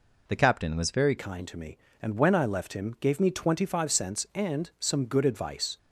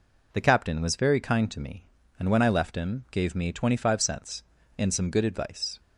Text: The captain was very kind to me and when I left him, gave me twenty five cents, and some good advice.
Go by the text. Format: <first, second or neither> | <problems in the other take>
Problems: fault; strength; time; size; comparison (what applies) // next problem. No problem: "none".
second | changes voice at "kind"; from 1.1 s on; 4.6 s long